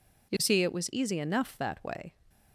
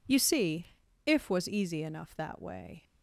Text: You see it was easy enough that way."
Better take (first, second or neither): first